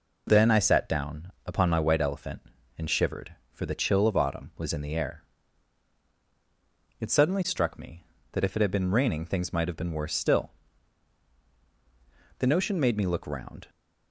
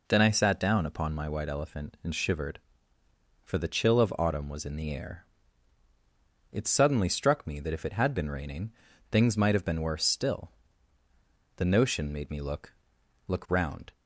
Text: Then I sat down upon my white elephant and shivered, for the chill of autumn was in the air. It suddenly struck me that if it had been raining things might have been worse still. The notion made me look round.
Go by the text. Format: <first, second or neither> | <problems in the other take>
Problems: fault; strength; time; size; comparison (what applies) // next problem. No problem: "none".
first | pauses between "raining" and "things"; at 8.7 s; 0.40 s long // says "look" twice; at 13.2 s